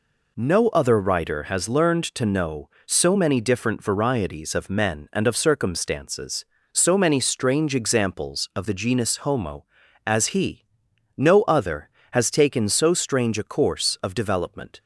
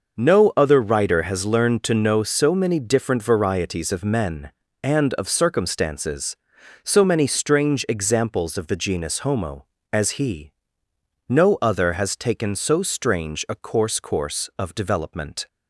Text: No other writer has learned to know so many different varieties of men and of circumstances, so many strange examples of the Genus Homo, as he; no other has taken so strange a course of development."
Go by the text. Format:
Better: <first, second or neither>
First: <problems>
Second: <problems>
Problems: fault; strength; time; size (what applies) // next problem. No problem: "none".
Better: first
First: none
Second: says "course" twice; at 14.0 s